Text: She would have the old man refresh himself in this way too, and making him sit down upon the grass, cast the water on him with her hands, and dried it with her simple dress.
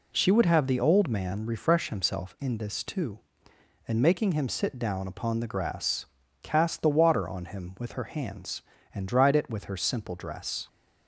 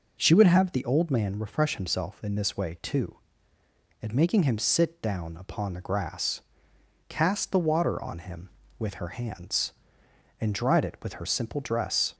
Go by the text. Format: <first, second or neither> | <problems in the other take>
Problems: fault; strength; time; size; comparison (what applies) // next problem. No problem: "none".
second | skips "way"; at 2.8 s